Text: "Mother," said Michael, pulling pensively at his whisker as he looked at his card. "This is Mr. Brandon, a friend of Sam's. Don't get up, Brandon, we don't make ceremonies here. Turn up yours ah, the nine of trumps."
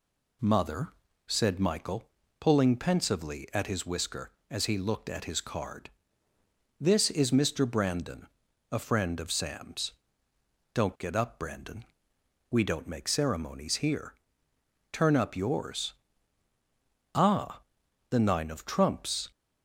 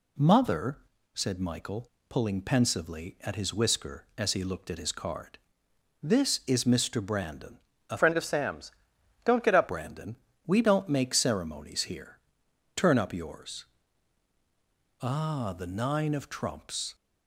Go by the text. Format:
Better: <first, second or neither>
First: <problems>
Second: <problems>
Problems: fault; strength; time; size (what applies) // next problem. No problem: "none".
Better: first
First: pauses between "yours" and "ah"; at 15.9 s; 1.2 s long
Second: changes voice from "friend" to "up"; from 7.9 to 9.6 s; 1.7 s long // pauses between "yours" and "ah"; strong; at 13.6 s; 1.3 s long